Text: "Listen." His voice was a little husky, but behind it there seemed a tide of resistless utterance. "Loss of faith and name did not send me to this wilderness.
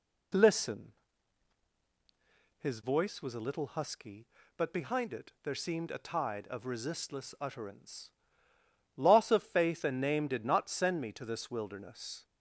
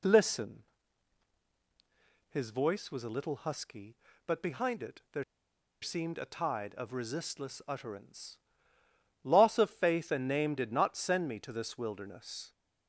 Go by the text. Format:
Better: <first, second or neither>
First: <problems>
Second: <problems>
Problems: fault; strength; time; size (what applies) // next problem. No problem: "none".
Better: first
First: none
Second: pauses between "there" and "seemed"; noticeable; at 5.2 s; 0.58 s long